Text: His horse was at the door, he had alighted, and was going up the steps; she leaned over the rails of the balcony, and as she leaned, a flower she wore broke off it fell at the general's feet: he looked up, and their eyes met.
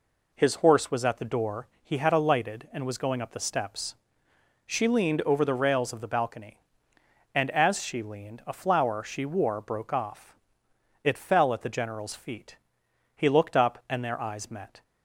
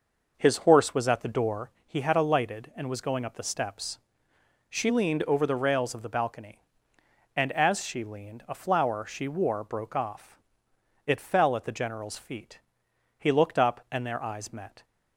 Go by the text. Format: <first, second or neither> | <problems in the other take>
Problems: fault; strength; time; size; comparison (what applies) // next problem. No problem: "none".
first | starts louder than the rest; noticeable; until 1.7 s; 5.5 dB // pauses between "off" and "it"; noticeable; at 10.3 s; 0.66 s long; noticeable in the first